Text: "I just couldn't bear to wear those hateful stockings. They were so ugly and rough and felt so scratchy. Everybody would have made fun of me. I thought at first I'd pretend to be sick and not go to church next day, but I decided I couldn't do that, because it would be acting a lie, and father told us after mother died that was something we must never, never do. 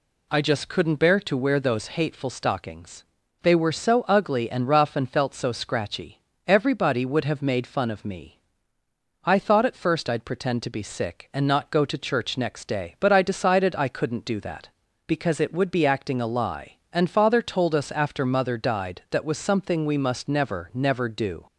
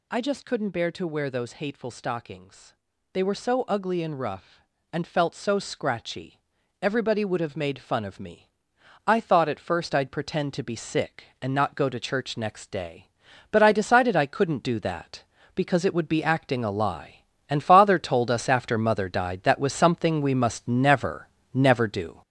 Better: first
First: none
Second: gets louder; throughout; 6.5 dB

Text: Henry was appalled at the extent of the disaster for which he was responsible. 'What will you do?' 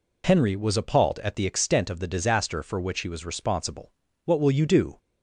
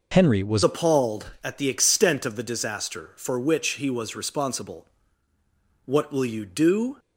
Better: first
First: none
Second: changes voice at "appalled"; from 0.6 s on; 6.3 s long

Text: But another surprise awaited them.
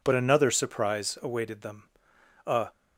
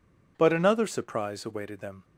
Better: second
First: goes on to say "A"; slight; from 2.4 s on; 0.22 s long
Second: none

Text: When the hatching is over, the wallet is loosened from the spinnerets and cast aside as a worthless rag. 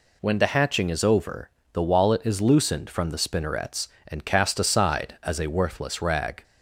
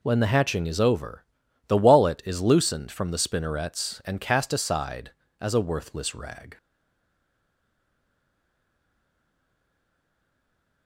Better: first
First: none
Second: stays silent after the last word; strong; from 6.5 s on; 4.3 s long

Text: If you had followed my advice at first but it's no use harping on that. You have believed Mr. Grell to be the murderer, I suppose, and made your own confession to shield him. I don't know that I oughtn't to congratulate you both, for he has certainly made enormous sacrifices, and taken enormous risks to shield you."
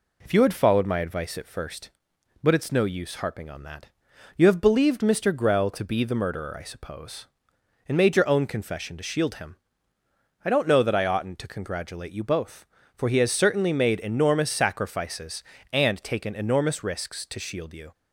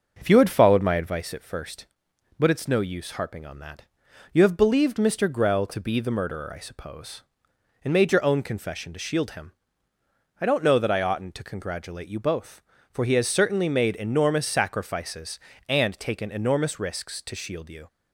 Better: first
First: none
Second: starts louder than the rest; noticeable; until 1.3 s; 6 dB

